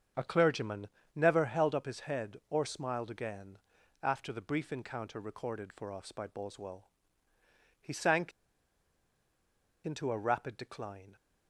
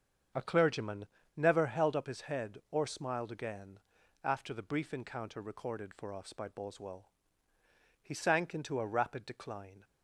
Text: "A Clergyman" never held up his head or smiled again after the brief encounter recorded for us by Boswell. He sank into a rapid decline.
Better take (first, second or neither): second